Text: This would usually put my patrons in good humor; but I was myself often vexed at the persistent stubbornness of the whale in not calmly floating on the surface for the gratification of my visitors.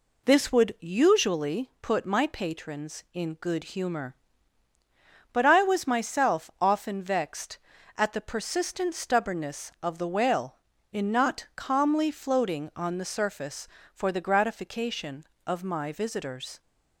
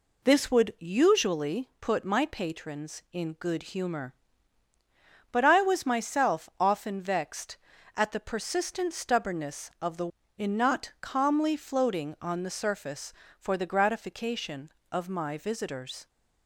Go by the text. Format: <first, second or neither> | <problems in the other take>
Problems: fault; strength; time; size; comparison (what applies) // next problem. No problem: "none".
first | skips "whale"; at 10.2 s